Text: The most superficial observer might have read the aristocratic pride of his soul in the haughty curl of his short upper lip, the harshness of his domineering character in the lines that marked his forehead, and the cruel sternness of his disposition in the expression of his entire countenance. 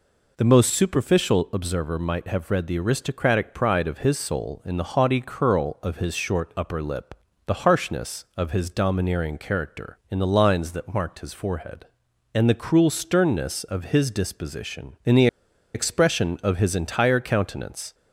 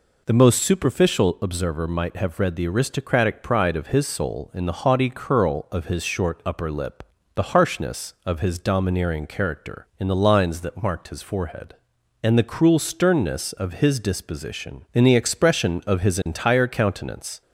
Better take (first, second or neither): second